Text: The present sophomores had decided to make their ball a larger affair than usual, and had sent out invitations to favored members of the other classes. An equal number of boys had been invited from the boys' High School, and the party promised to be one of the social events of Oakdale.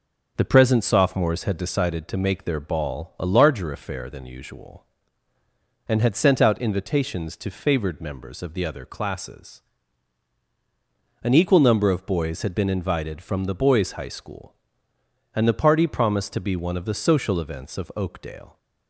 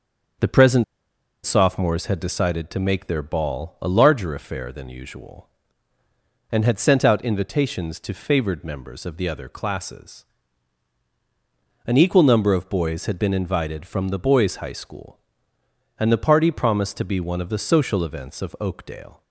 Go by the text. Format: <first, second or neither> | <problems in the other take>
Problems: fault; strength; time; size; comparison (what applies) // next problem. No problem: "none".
first | pauses between "present" and "sophomores"; noticeable; at 0.8 s; 0.61 s long